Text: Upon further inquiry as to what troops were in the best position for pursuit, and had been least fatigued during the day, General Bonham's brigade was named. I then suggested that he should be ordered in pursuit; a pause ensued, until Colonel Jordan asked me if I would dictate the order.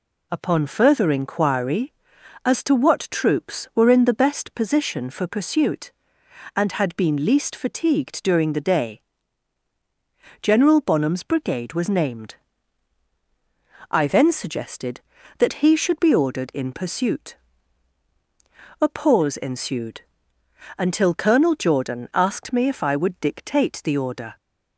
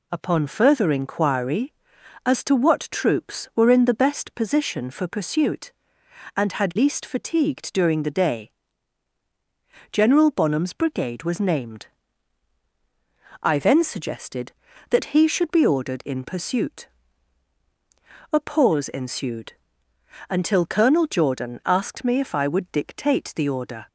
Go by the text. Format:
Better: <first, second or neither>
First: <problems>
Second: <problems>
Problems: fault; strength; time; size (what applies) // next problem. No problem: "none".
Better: first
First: none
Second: skips "been"; at 6.7 s